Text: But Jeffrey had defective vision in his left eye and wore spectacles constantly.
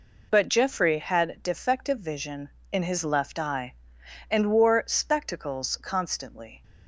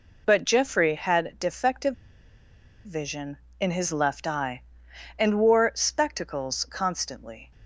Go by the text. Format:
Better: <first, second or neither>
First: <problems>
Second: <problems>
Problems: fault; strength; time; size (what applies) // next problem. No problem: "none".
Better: first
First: none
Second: pauses between "defective" and "vision"; noticeable; at 1.9 s; 0.90 s long